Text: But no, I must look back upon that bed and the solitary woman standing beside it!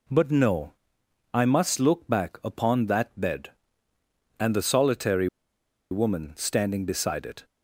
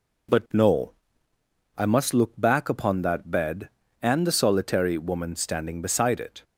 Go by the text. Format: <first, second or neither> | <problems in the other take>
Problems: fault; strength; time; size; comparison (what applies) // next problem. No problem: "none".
second | pauses between "solitary" and "woman"; noticeable; at 5.2 s; 0.64 s long